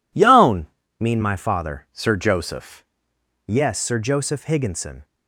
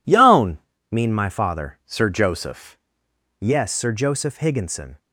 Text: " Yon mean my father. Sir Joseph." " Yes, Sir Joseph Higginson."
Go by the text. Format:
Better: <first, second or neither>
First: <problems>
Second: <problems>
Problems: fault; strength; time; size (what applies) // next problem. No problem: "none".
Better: neither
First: pauses between "Yon" and "mean"; slight; at 0.6 s; 0.32 s long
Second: pauses between "Yon" and "mean"; slight; at 0.5 s; 0.32 s long